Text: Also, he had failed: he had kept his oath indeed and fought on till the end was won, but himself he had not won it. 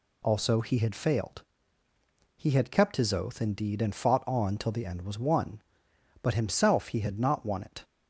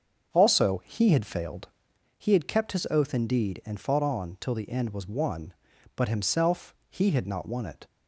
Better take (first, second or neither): first